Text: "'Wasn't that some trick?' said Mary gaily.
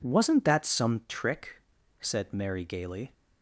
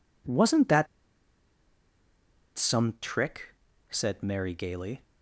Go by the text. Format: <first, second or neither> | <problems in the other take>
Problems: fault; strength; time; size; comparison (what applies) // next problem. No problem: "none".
first | pauses between "that" and "some"; strong; at 0.8 s; 1.7 s long